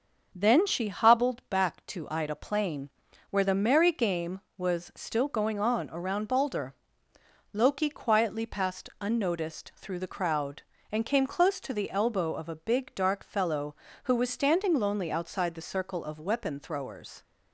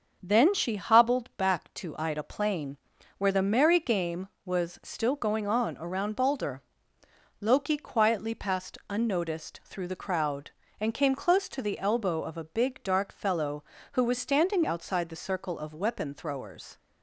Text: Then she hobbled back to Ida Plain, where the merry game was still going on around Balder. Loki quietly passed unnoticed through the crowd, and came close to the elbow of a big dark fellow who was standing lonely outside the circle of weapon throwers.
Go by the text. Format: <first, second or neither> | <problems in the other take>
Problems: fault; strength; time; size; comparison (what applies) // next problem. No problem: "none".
first | starts louder than the rest; until 1.2 s; 6.5 dB; also in the first // skips "lonely"; at 14.6 s